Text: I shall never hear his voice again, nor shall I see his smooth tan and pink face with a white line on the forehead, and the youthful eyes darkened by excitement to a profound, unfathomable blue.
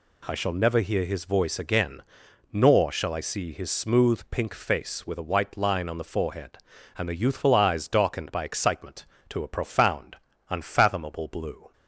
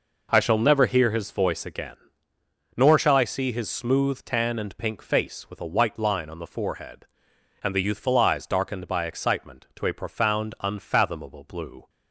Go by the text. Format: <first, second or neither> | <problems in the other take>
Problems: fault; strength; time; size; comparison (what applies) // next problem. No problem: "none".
second | skips "tan and"; at 4.2 s